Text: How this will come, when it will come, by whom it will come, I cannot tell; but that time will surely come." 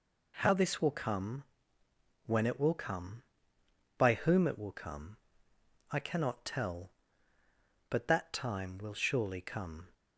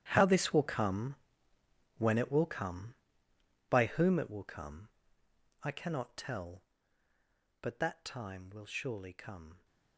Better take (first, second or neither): first